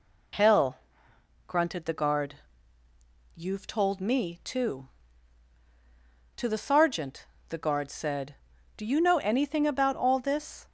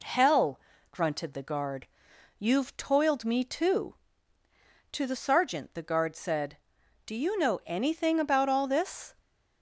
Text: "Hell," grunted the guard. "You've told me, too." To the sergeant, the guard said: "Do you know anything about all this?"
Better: first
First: none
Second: says "toiled" for "told"; at 2.7 s

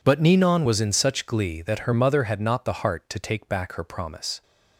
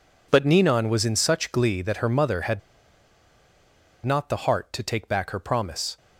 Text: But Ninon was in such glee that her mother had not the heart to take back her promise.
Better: first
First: none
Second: pauses between "had" and "not"; strong; at 2.6 s; 1.4 s long

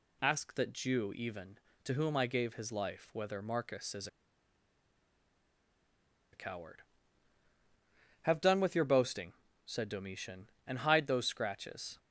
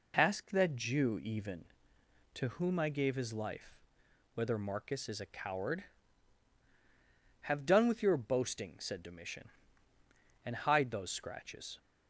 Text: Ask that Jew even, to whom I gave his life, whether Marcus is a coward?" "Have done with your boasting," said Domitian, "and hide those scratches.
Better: second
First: pauses between "is" and "a"; strong; at 4.0 s; 2.2 s long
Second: none

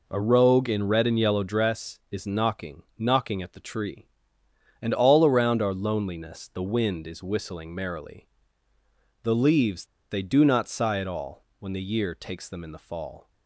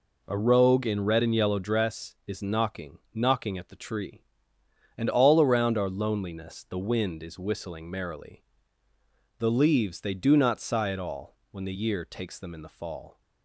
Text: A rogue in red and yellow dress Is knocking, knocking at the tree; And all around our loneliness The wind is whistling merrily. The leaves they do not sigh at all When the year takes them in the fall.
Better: second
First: pauses between "leaves" and "they"; slight; at 9.8 s; 0.24 s long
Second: none

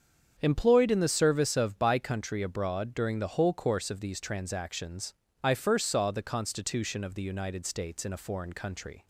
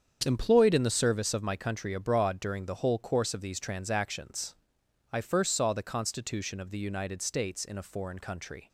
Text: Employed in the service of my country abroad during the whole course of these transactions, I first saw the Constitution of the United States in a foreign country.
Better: second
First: starts louder than the rest; strong; until 1.4 s; 7.5 dB // says "by" for "my"; at 1.7 s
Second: starts louder than the rest; strong; until 1.2 s; 7.5 dB

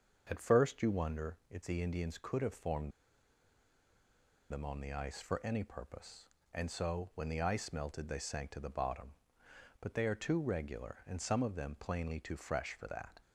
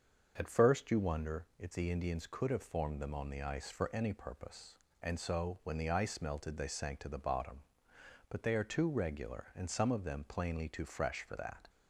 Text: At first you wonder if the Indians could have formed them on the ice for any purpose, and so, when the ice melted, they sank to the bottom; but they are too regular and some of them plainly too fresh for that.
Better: second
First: starts louder than the rest; until 1.3 s; 7 dB // pauses between "formed" and "them"; strong; at 2.9 s; 1.5 s long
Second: starts louder than the rest; until 1.3 s; 7 dB

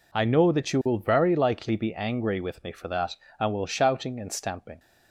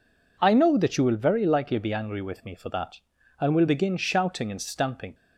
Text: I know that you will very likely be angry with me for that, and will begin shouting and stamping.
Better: second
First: skips "begin"; at 3.6 s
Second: none

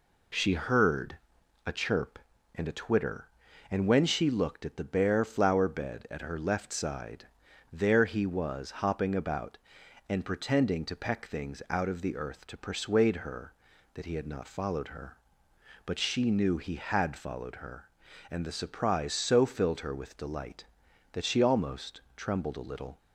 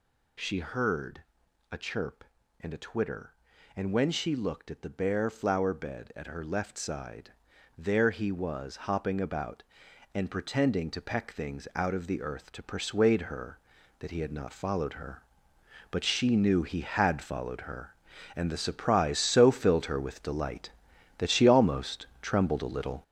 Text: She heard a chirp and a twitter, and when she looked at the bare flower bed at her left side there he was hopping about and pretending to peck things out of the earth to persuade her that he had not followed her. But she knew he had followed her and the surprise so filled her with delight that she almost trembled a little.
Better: first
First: pauses between "heard" and "a"; at 1.1 s; 0.44 s long // pauses between "side" and "there"; at 7.2 s; 0.44 s long // pauses between "almost" and "trembled"; slight; at 22.0 s; 0.16 s long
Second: gets louder; strong; throughout; 7.5 dB // pauses between "heard" and "a"; at 1.2 s; 0.44 s long // pauses between "side" and "there"; at 7.3 s; 0.44 s long // pauses between "almost" and "trembled"; slight; at 22.0 s; 0.16 s long

